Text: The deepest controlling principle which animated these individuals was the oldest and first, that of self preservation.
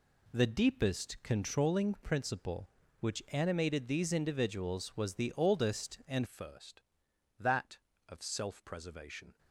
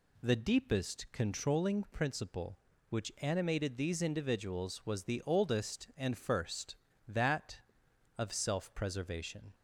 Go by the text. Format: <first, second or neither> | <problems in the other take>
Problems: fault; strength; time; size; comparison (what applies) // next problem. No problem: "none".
second | changes voice at "first"; from 6.2 s on; 3.1 s long